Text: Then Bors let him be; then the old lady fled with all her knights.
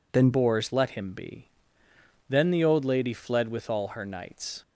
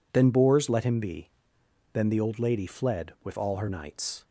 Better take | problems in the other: second | changes voice at "Bors"; from 0.3 s on; 4.3 s long

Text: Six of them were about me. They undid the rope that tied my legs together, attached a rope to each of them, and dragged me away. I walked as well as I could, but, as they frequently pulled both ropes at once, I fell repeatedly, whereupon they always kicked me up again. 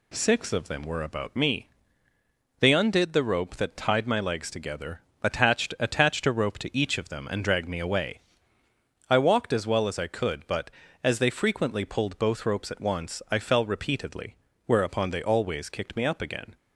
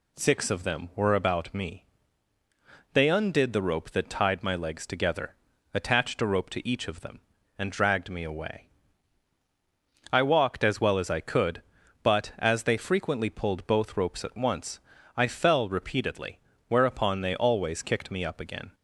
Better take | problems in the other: second | says "attached" twice; at 5.7 s

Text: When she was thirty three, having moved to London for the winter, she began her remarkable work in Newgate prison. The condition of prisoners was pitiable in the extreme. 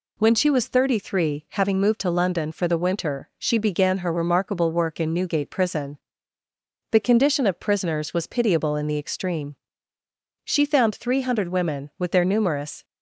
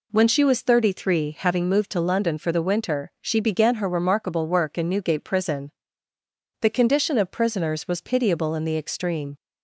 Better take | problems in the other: second | goes on to say "She found three hundred women with their numerous"; strong; from 10.4 s on; 2.4 s long

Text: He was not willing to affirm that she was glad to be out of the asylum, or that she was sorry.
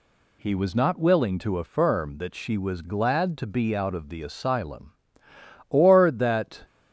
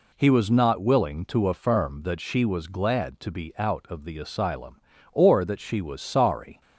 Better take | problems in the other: second | stops before "she was sorry"; at 6.6 s

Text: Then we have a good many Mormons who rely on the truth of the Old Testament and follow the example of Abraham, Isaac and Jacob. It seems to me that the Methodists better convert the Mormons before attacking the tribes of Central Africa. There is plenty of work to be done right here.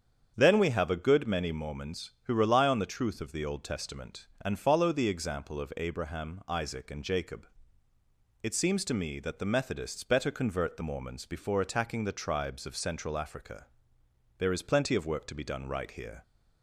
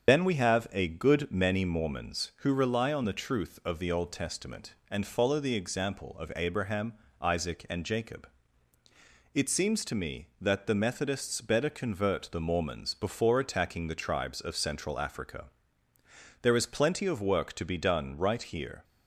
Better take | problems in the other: first | loses the start of "Then"; at 0.0 s; 110 ms // starts louder than the rest; strong; until 1.1 s; 7 dB; strong in the first

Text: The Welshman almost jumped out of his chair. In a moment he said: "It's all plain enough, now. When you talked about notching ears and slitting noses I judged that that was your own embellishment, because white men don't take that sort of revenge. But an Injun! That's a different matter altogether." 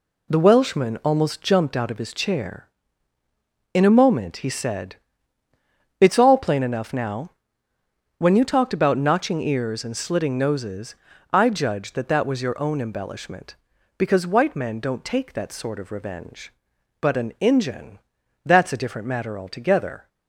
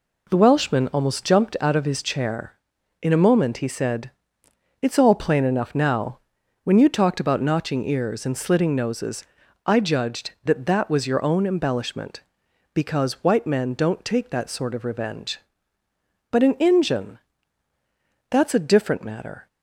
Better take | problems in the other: first | pauses between "noses" and "I"; at 9.2 s; 0.42 s long; also in the first // stops before "altogether"; at 19.4 s

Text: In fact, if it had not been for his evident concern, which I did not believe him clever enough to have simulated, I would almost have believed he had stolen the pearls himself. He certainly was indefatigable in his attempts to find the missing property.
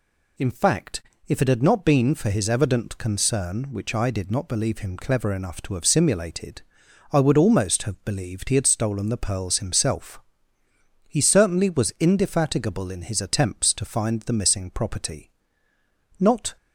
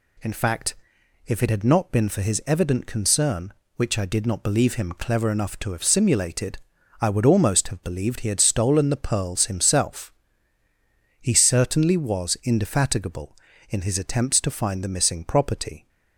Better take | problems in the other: second | goes on to say "Not"; slight; from 16.2 s on; 0.36 s long

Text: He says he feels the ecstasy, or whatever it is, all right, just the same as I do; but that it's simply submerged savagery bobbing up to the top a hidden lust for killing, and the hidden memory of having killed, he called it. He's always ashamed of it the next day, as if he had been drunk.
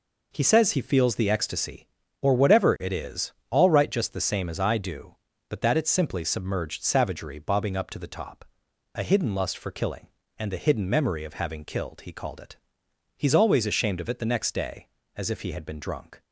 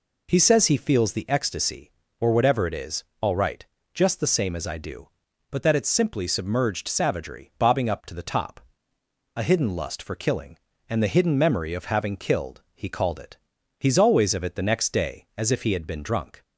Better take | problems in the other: first | pauses between "top" and "a"; noticeable; at 8.5 s; 0.78 s long; noticeable in the first // skips "ashamed"; at 14.3 s

